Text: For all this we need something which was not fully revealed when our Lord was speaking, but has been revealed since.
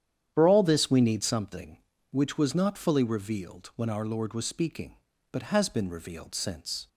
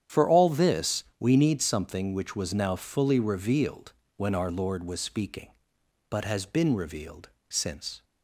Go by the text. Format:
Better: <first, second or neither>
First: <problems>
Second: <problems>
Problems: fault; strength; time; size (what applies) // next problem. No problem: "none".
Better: first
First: starts louder than the rest; strong; until 1.3 s; 9.5 dB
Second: starts louder than the rest; strong; until 1.2 s; 9.5 dB // pauses between "this" and "we"; slight; at 1.0 s; 0.16 s long // says "now" for "not"; at 2.5 s // pauses between "revealed" and "when"; slight; at 3.9 s; 0.24 s long // pauses between "revealed" and "since"; slight; at 7.2 s; 0.20 s long